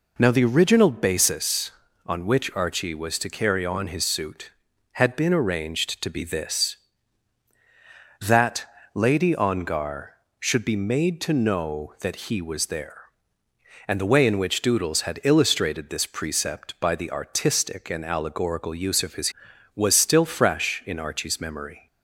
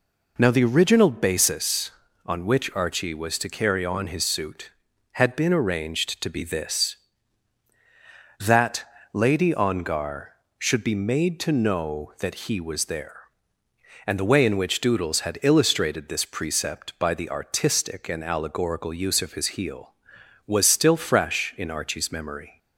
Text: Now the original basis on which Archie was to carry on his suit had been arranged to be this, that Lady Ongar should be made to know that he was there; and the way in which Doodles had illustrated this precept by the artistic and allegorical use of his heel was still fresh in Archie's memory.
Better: second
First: pauses between "that" and "Lady"; slight; at 8.6 s; 0.28 s long // skips "heel"; at 19.5 s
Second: pauses between "that" and "Lady"; slight; at 8.8 s; 0.28 s long

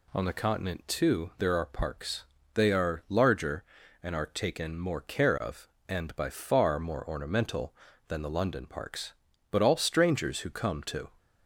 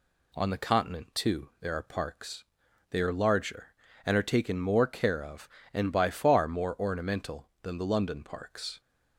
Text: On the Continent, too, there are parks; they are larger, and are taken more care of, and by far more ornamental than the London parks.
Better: second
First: goes on to say "But all strangers who come to"; from 9.5 s on; 1.5 s long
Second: none

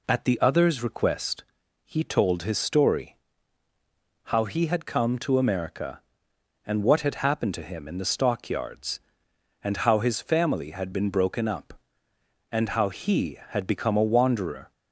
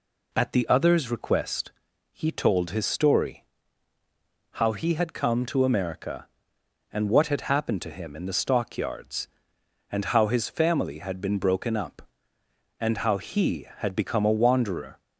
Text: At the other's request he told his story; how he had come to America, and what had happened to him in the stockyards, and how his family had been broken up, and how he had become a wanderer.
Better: neither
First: pauses between "request" and "he"; at 1.4 s; 0.42 s long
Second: pauses between "request" and "he"; at 1.7 s; 0.42 s long

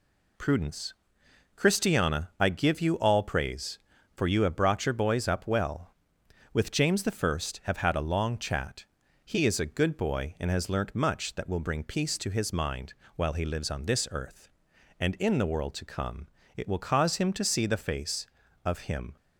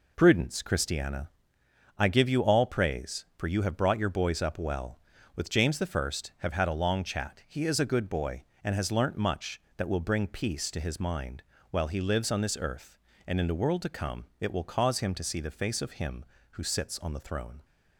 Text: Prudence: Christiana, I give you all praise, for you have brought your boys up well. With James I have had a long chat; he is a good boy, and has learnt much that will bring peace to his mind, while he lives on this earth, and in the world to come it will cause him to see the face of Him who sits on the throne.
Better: second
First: pauses between "come" and "it"; slight; at 16.2 s; 0.28 s long // stops before "who sits on the throne"; at 19.1 s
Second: none

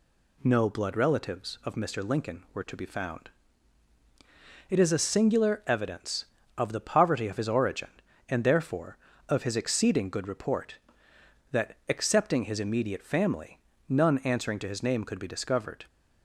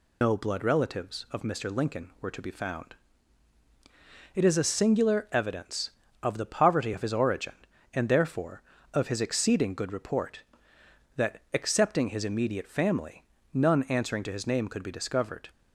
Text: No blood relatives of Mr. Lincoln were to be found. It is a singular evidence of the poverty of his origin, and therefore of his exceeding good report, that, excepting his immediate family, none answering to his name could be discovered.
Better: first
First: none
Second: loses the start of "No"; at 0.2 s; 135 ms

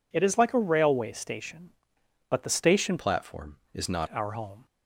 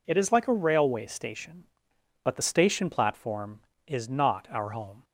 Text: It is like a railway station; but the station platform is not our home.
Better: second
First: changes voice from "platform" to "not"; from 2.9 to 4.0 s; 1.1 s long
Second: none

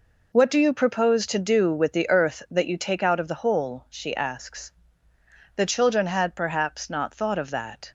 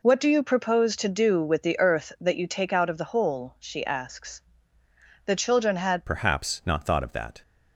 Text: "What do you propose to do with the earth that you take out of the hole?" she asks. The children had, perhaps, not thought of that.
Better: first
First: none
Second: changes voice at "perhaps"; from 6.0 s on; 1.4 s long

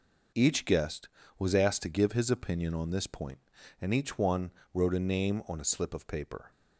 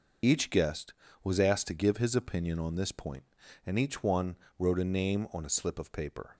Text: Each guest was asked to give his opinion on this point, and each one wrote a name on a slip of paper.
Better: first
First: pauses between "one" and "wrote"; slight; at 4.5 s; 0.22 s long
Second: loses the start of "Each"; at 0.2 s; 40 ms // pauses between "one" and "wrote"; slight; at 4.3 s; 0.22 s long

